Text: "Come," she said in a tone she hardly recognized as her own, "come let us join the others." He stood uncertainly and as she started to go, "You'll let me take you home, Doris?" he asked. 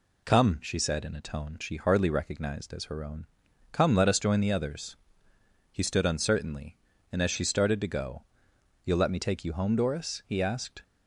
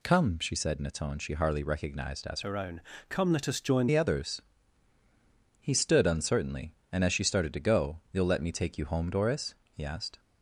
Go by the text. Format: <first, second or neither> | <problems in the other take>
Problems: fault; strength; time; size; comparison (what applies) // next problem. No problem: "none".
first | changes voice from "her" to "join"; from 2.4 to 3.8 s; 1.4 s long